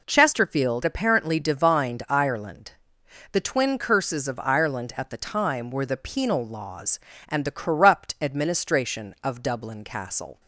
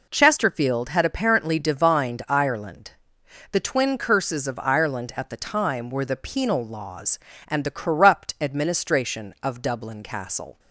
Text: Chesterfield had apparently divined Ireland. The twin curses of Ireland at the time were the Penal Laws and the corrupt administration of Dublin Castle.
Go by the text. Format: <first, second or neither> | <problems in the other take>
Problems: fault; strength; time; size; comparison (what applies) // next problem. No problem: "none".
second | skips "had"; at 0.8 s